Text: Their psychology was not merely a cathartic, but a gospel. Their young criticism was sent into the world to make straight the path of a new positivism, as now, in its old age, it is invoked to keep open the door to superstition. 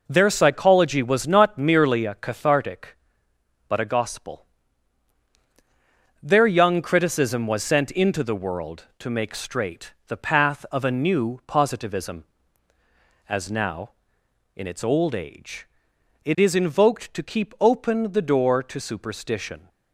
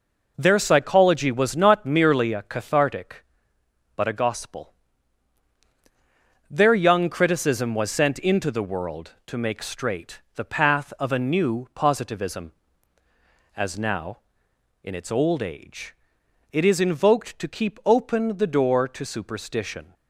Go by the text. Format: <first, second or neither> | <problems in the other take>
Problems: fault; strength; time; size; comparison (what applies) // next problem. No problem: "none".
neither | none